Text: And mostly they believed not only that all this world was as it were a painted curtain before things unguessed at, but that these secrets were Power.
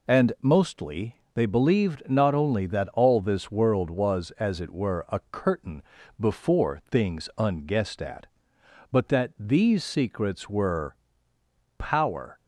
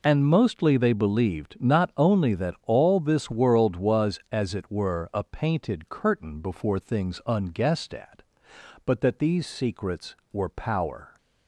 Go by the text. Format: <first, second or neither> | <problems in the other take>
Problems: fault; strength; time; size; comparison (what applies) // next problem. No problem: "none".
second | pauses between "mostly" and "they"; slight; at 1.1 s; 0.18 s long // skips "painted"; at 5.2 s // pauses between "curtain" and "before"; at 5.8 s; 0.38 s long // pauses between "were" and "Power"; noticeable; at 10.9 s; 0.84 s long